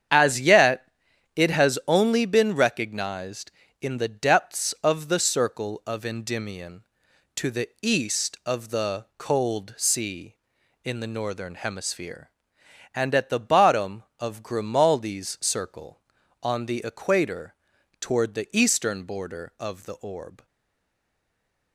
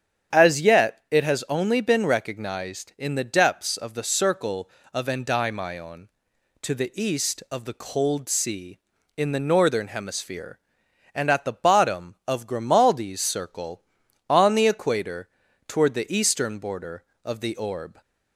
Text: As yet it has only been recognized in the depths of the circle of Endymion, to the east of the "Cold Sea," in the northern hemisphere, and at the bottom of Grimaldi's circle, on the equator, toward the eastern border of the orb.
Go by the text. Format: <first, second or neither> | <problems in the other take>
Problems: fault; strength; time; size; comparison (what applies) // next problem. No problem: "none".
second | starts louder than the rest; strong; until 1.5 s; 8.5 dB; strong in the second // pauses between "yet" and "it"; noticeable; at 0.8 s; 0.48 s long // stays silent after the last word; noticeable; from 20.4 s on; 1.3 s long